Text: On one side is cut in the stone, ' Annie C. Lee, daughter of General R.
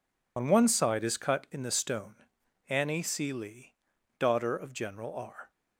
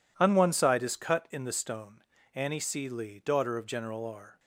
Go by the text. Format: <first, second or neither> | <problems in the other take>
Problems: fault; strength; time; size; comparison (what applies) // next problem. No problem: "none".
second | loses the start of "On"; at 0.3 s; 60 ms